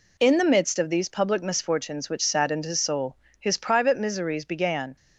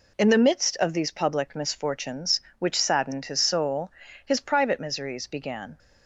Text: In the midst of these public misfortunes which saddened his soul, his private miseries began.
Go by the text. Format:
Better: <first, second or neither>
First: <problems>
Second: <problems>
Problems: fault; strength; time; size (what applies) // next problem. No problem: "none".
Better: neither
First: none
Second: none